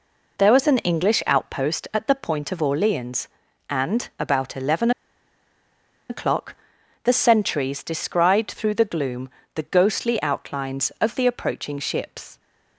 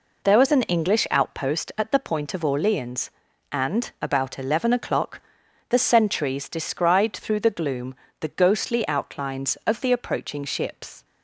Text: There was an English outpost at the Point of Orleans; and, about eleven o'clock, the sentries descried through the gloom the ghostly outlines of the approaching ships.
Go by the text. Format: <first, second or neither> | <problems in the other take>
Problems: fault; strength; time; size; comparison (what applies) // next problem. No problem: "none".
second | pauses between "eleven" and "o'clock"; at 4.9 s; 1.1 s long // pauses between "gloom" and "the"; slight; at 9.2 s; 0.24 s long; slight in the second